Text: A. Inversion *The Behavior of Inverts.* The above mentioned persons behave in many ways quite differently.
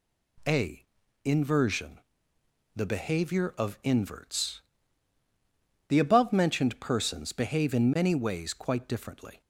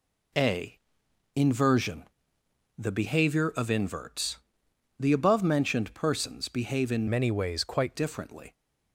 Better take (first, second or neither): first